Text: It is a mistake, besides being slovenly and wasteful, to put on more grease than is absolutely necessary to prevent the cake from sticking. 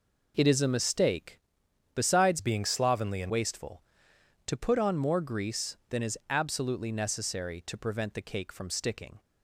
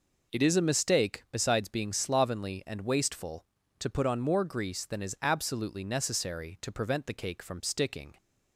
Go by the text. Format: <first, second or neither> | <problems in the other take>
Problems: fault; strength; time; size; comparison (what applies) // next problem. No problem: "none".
second | changes voice from "being" to "and"; from 2.3 to 3.2 s; 0.9 s long